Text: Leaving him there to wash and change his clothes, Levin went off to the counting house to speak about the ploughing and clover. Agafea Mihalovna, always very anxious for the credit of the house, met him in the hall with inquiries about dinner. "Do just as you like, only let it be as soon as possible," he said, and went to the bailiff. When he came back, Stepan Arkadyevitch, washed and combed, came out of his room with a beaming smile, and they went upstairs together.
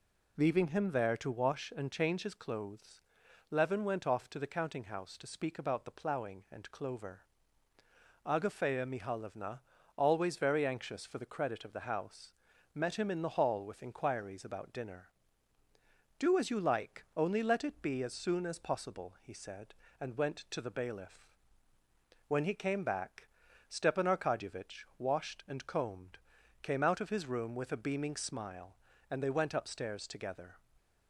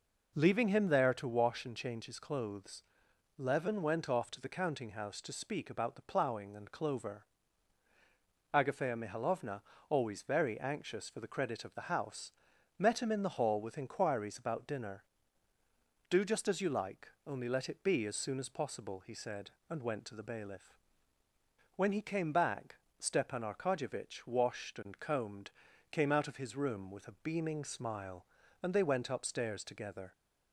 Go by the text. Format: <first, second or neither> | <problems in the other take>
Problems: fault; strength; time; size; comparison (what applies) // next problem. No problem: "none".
second | skips "just"; at 16.3 s